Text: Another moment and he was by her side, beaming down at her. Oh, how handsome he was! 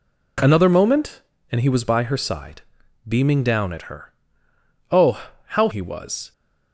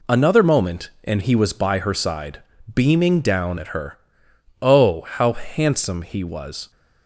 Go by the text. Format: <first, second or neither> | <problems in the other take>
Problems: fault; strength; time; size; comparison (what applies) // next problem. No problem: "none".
second | skips "handsome"; at 5.6 s